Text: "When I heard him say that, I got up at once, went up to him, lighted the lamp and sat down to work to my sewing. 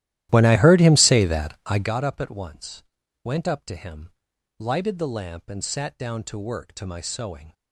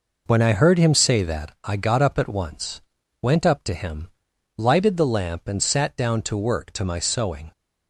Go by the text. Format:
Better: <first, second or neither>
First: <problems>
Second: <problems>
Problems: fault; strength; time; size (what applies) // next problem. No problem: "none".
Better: second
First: starts louder than the rest; strong; until 1.9 s; 14 dB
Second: none